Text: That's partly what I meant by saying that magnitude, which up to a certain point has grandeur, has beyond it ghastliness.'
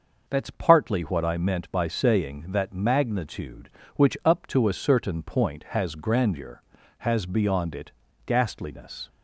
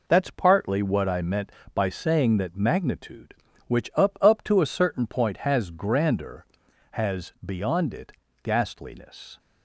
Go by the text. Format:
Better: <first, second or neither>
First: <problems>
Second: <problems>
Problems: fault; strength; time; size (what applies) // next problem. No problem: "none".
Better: first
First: pauses between "it" and "ghastliness"; slight; at 7.9 s; 0.32 s long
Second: says "up" twice; at 4.2 s // pauses between "it" and "ghastliness"; slight; at 8.1 s; 0.30 s long